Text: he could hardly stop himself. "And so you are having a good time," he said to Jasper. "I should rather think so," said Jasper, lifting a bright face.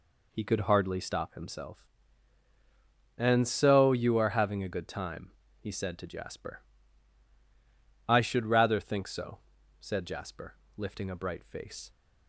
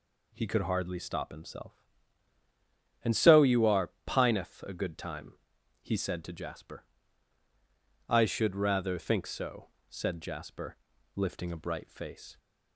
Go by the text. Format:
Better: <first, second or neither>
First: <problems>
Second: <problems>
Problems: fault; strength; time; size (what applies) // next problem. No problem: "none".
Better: first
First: none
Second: says "pineth" for "having"; at 4.0 s